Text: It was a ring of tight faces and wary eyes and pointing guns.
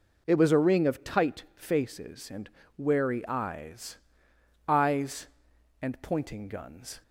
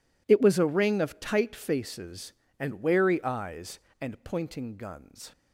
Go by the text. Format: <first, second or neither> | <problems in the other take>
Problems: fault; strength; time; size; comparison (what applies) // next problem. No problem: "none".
second | pauses between "and" and "wary"; slight; at 2.4 s; 0.30 s long // says "eyes" twice; at 4.6 s